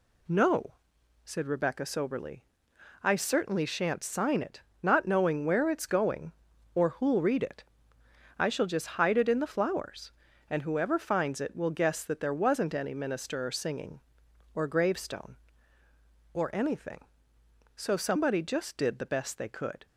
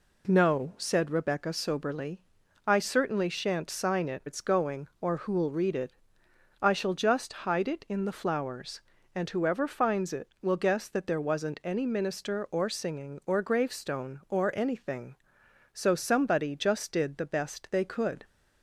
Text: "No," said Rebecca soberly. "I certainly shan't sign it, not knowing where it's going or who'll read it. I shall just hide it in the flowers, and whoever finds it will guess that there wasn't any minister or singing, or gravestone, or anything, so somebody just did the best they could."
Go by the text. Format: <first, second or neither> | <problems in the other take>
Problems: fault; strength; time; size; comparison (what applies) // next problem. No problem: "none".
first | skips "not knowing where"; at 4.2 s